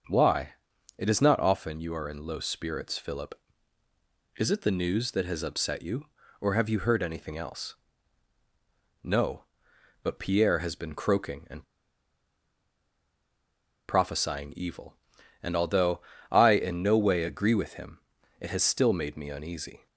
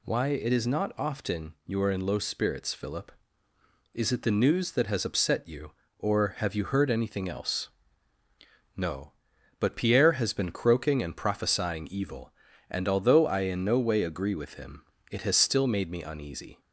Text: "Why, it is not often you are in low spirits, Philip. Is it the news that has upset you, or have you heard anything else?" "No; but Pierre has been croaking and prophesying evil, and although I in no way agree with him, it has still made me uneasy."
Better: second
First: starts louder than the rest; noticeable; until 1.5 s; 6 dB // pauses between "and" and "prophesying"; strong; at 11.6 s; 2.2 s long // pauses between "although" and "I"; slight; at 16.0 s; 0.28 s long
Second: none

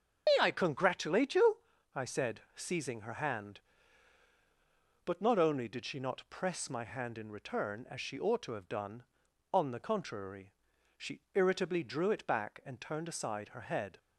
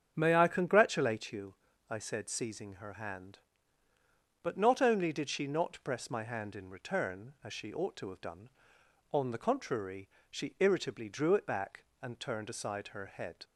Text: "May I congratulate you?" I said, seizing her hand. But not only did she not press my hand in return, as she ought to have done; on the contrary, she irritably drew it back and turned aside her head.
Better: second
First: loses the start of "May"; at 0.2 s; 95 ms // starts louder than the rest; strong; until 1.2 s; 7 dB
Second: starts louder than the rest; strong; until 1.1 s; 8 dB

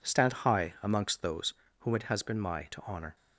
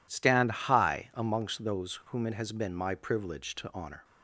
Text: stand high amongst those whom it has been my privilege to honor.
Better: second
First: pauses between "those" and "whom"; slight; at 1.5 s; 0.26 s long // skips "privilege"; at 2.6 s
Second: none

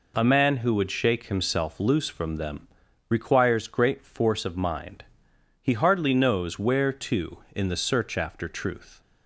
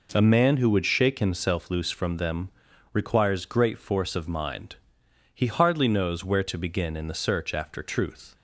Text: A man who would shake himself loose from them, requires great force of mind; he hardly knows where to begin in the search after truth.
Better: second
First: skips "begin"; at 7.4 s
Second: none

